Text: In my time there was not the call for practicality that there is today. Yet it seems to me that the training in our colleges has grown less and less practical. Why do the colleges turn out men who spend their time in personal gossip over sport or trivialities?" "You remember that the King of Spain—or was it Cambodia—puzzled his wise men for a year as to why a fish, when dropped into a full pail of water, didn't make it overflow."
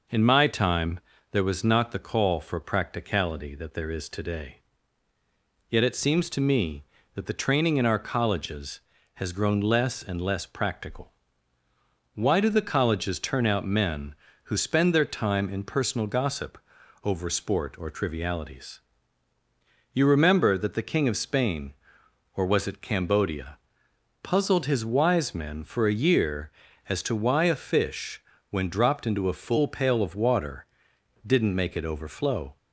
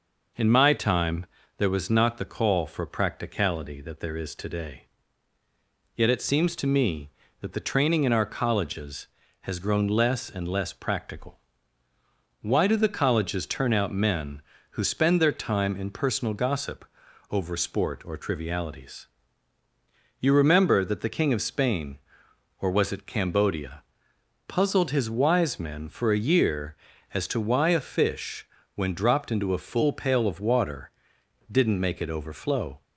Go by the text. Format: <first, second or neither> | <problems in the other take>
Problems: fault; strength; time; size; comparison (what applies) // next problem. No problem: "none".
neither | pauses between "time" and "there"; slight; the same in both // pauses between "gossip" and "over"; noticeable; the same in both